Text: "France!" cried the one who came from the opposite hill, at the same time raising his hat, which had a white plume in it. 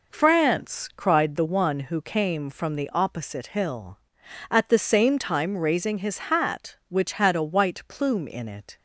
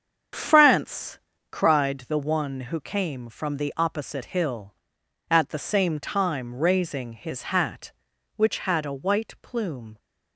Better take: first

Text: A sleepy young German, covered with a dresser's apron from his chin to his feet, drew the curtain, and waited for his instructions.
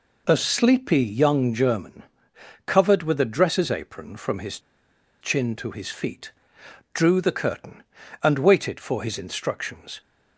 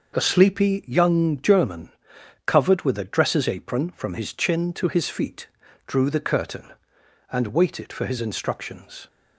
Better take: second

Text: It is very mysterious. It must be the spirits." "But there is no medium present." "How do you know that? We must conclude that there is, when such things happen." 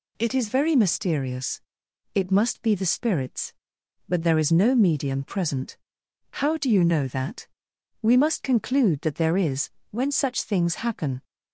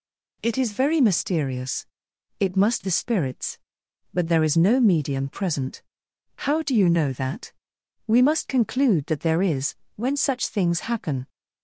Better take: first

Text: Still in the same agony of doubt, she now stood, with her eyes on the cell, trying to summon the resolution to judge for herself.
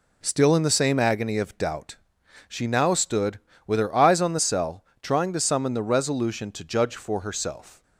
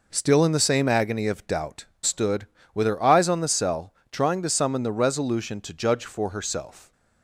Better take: first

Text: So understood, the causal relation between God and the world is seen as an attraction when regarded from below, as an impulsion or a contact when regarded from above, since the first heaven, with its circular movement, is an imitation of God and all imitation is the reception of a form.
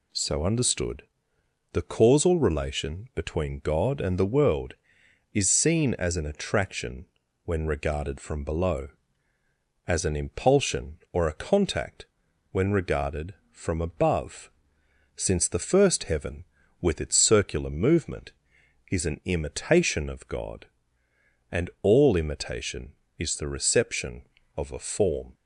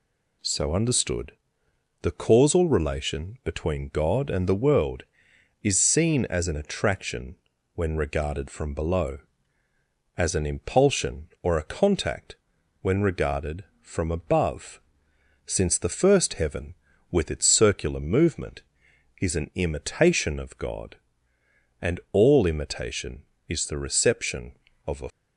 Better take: first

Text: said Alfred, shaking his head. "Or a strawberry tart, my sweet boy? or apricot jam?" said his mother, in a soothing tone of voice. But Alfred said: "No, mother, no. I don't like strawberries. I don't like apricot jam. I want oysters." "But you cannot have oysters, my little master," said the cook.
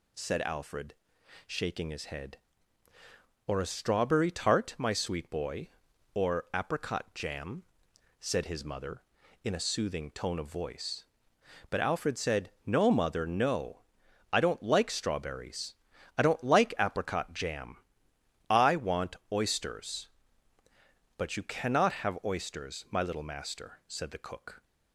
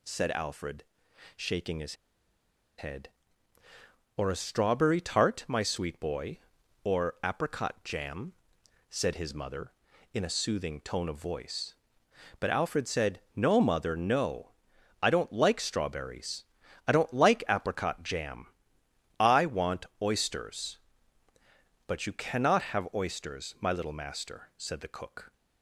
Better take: first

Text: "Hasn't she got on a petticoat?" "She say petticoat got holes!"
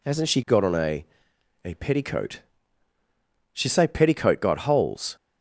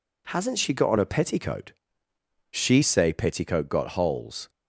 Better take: second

